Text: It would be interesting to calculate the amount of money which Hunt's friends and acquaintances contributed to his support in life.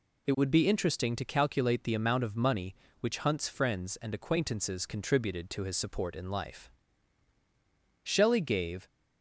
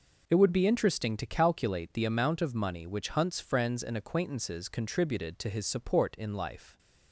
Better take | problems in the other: second | goes on to say "Shelley gave"; noticeable; from 8.0 s on; 0.84 s long

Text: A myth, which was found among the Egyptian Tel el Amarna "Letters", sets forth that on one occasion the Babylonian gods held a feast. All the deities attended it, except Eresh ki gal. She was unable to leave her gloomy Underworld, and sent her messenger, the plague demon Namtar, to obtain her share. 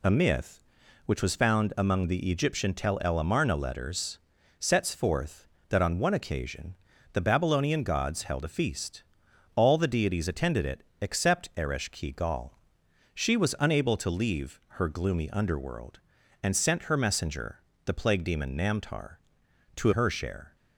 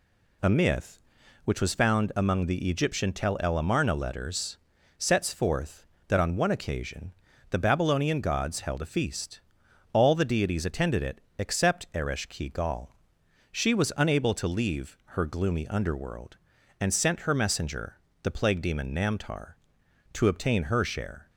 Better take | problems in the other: second | pauses between "occasion" and "the"; at 6.7 s; 0.38 s long; also in the second // pauses between "leave" and "her"; slight; at 14.5 s; 0.20 s long; slight in the second // skips "obtain"; at 19.9 s

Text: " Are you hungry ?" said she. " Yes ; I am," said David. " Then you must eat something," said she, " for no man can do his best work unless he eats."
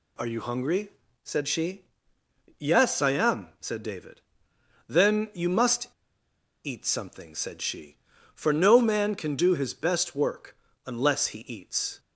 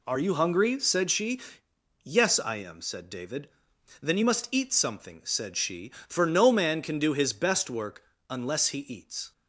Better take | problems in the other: second | pauses between "must" and "eat"; noticeable; at 5.8 s; 0.74 s long // pauses between "work" and "unless"; slight; at 10.5 s; 0.30 s long; slight in the second

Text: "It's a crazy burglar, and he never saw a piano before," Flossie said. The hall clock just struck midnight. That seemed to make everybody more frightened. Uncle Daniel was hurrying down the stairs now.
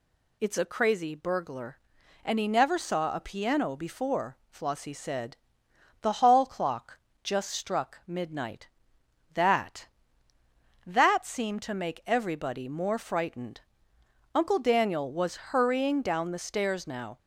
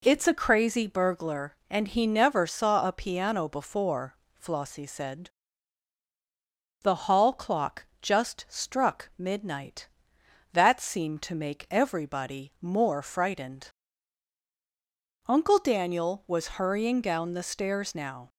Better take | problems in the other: second | pauses between "clock" and "just"; slight; at 6.9 s; 0.24 s long; slight in the second // says "That" twice; at 10.8 s

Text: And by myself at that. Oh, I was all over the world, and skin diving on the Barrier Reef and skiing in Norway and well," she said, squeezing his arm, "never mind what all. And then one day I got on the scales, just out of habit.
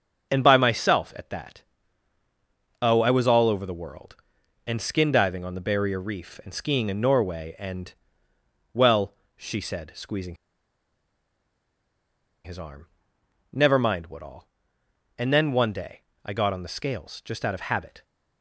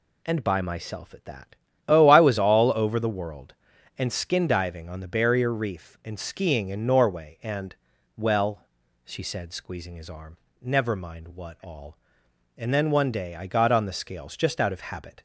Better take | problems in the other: second | starts louder than the rest; noticeable; until 1.3 s; 6 dB // pauses between "and" and "well"; noticeable; at 7.9 s; 0.80 s long; also in the second // pauses between "squeezing" and "his"; strong; at 10.3 s; 2.0 s long // pauses between "day" and "I"; slight; at 16.0 s; 0.22 s long

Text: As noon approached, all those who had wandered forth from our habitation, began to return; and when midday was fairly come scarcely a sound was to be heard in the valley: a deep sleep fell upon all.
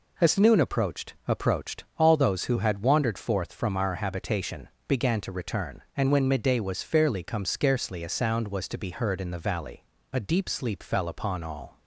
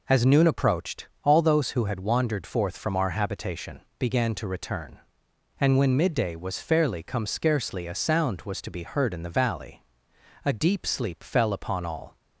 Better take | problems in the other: second | says "approached" twice; at 1.2 s

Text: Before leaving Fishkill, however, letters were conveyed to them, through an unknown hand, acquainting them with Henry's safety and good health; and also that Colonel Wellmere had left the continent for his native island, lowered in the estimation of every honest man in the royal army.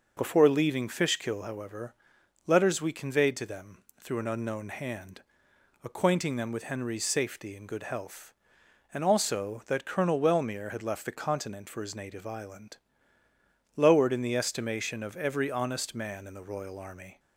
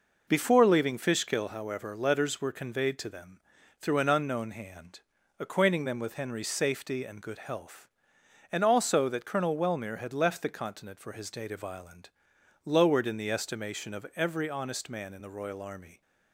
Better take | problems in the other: second | says "we" for "were"; at 2.8 s

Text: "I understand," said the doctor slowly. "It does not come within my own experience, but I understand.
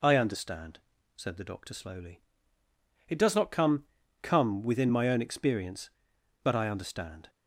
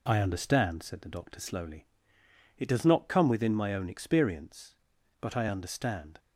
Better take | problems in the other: second | says "come" twice; at 4.2 s

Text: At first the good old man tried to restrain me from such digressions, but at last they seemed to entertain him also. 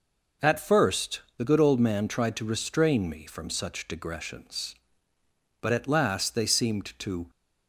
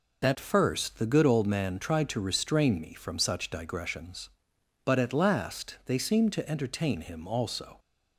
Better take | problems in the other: second | pauses between "first" and "the"; slight; at 1.1 s; 0.18 s long // stops before "entertain him also"; at 7.2 s

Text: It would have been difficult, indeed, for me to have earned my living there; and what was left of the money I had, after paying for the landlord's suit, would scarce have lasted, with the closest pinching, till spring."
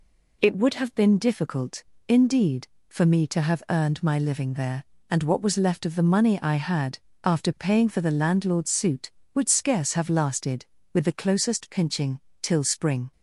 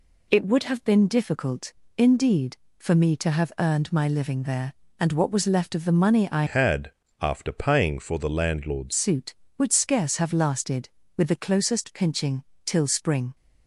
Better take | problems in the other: first | changes voice from "had" to "landlord's"; from 6.4 to 8.9 s; 2.5 s long

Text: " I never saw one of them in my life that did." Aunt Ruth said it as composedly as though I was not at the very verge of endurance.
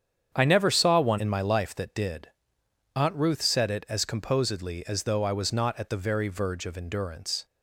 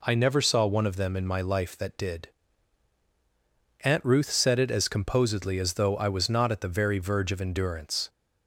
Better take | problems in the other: second | starts louder than the rest; strong; until 1.3 s; 8.5 dB // skips "of them"; at 1.1 s

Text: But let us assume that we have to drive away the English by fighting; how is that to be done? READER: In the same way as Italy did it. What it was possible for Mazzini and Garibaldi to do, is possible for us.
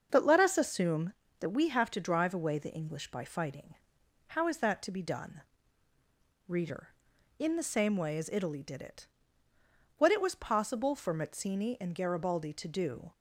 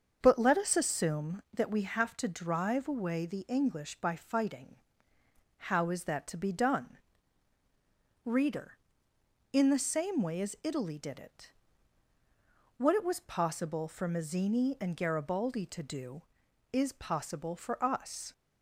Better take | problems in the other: second | starts louder than the rest; until 1.1 s; 6.5 dB; also in the second // stops before "is possible for us"; at 13.1 s

